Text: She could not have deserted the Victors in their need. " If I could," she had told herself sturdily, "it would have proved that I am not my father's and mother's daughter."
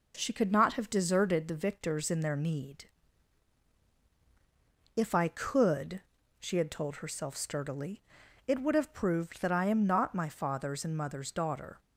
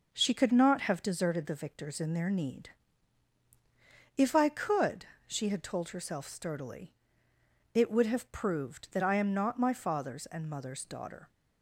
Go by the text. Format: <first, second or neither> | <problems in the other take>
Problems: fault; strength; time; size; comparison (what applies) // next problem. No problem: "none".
neither | none